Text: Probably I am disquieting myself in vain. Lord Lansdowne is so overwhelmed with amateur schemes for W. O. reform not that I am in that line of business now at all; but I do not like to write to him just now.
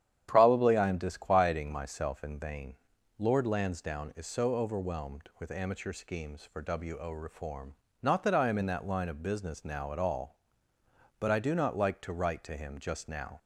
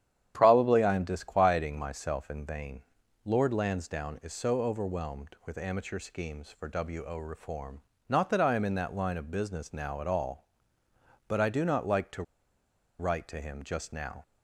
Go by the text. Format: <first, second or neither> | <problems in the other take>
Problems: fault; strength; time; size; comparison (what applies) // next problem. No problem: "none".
first | starts louder than the rest; strong; until 1.3 s; 9.5 dB; strong in the first // pauses between "reform" and "not"; slight; at 7.7 s; 0.30 s long; slight in the first // pauses between "to" and "write"; noticeable; at 12.2 s; 0.77 s long